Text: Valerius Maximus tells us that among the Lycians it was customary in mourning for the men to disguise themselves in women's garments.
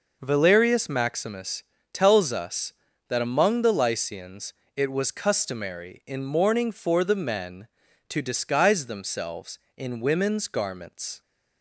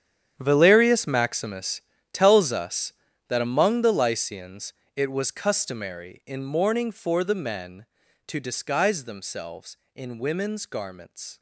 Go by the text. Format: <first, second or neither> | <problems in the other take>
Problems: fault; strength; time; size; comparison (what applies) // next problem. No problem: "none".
first | gets quieter; strong; throughout; 16 dB // pauses between "Maximus" and "tells"; slight; at 1.8 s; 0.32 s long; slight in the first // pauses between "Lycians" and "it"; slight; at 4.7 s; 0.20 s long; slight in the first